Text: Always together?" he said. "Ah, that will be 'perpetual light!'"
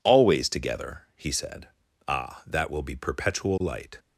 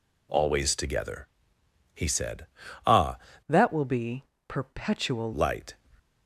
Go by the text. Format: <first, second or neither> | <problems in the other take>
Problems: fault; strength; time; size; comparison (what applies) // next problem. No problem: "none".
first | changes voice from "that" to "perpetual"; from 3.4 to 5.3 s; 1.9 s long // pauses between "be" and "perpetual"; slight; at 4.2 s; 0.22 s long